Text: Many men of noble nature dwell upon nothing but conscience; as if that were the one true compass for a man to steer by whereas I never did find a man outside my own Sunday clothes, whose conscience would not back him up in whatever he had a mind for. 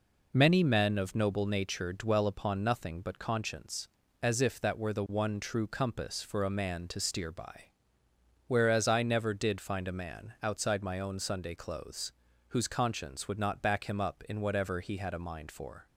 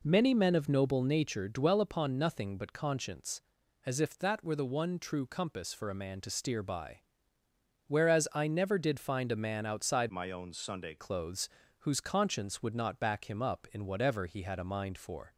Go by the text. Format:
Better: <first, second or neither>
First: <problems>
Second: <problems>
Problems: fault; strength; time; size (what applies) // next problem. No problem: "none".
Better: first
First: pauses between "by" and "whereas"; noticeable; at 7.6 s; 0.78 s long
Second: pauses between "by" and "whereas"; noticeable; at 6.9 s; 0.88 s long // changes voice from "my" to "Sunday"; from 10.0 to 10.9 s; 0.9 s long